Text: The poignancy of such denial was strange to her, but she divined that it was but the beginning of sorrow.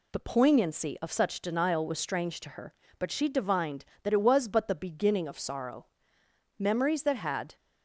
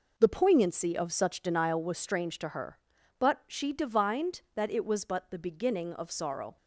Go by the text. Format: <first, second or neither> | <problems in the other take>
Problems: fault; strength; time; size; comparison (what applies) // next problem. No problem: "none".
second | goes on to say "Memories that had"; noticeable; from 6.5 s on; 0.98 s long